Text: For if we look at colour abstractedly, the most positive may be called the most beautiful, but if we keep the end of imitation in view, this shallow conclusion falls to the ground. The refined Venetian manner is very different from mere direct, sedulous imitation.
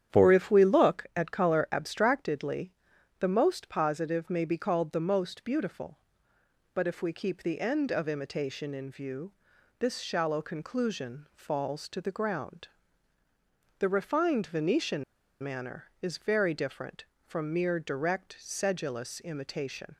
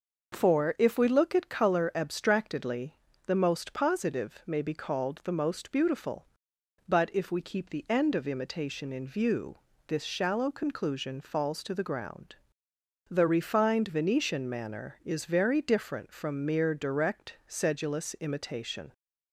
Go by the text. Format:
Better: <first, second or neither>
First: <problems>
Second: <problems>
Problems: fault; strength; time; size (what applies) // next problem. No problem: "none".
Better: second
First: starts louder than the rest; strong; until 1.2 s; 9.5 dB // pauses between "Venetian" and "manner"; at 15.0 s; 0.39 s long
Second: starts louder than the rest; noticeable; until 1.4 s; 6 dB